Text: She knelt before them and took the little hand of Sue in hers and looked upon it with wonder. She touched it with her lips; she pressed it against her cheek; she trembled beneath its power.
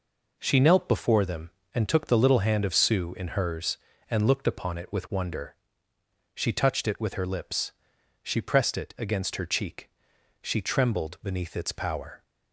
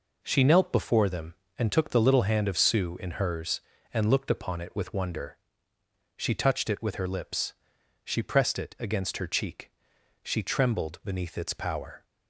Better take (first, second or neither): neither